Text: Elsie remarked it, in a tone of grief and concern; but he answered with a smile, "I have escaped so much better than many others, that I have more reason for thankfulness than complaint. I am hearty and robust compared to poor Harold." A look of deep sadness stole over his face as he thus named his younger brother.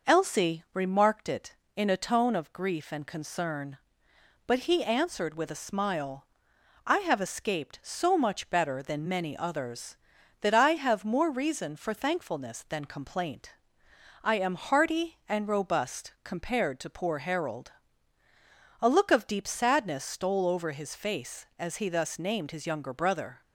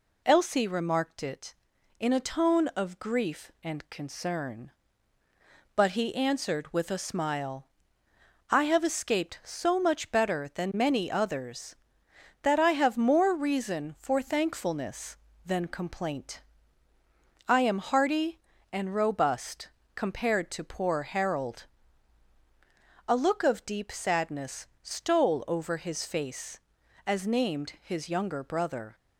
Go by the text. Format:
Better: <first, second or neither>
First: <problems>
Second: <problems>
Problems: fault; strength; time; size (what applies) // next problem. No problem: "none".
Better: first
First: none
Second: pauses between "robust" and "compared"; slight; at 19.7 s; 0.26 s long // skips "he thus"; at 27.2 s